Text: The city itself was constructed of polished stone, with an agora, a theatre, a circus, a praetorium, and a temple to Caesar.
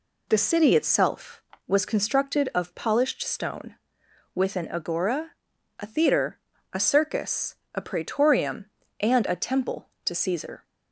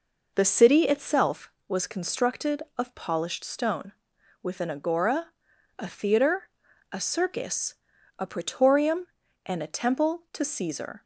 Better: neither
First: none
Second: none

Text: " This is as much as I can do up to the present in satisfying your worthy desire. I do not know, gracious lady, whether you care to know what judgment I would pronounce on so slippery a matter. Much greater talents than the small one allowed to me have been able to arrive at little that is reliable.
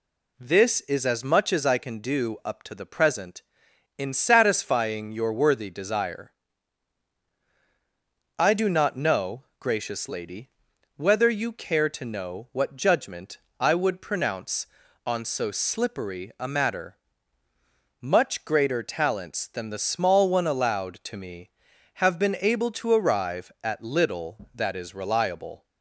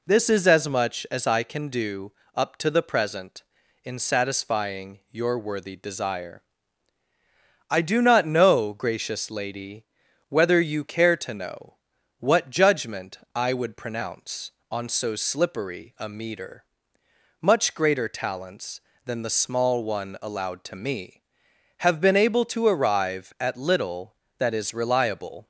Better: first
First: pauses between "judgment" and "I"; slight; at 13.3 s; 0.24 s long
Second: pauses between "do" and "up"; slight; at 2.1 s; 0.24 s long // pauses between "know" and "what"; at 11.7 s; 0.42 s long // pauses between "judgment" and "I"; slight; at 13.1 s; 0.16 s long // says "meter" for "matter"; at 16.0 s

